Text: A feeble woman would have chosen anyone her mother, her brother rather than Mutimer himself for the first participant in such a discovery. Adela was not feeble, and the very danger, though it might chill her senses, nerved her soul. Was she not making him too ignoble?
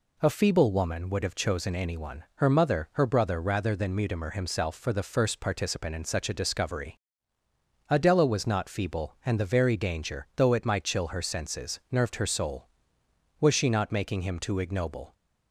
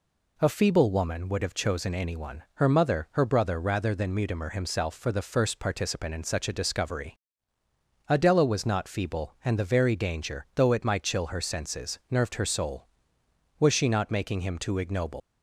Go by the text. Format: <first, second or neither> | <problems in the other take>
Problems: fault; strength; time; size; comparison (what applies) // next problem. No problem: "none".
first | leaves "ignoble" unfinished; at 15.2 s; 120 ms